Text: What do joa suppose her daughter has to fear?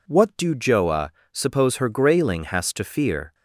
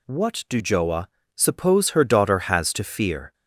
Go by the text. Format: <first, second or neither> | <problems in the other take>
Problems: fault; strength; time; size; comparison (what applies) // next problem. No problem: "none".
second | pauses between "joa" and "suppose"; slight; at 1.0 s; 0.22 s long; slight in the second // says "grayling" for "daughter"; at 1.8 s